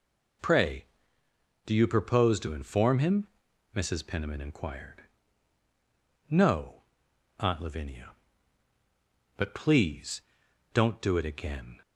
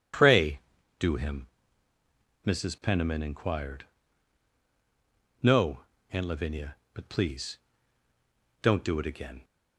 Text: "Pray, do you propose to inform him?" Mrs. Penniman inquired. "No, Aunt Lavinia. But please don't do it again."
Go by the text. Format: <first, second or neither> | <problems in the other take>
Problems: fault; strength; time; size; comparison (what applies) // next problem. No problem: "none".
first | skips "you propose to inform"; at 1.1 s // pauses between "please" and "don't"; at 7.5 s; 1.0 s long; noticeable in the first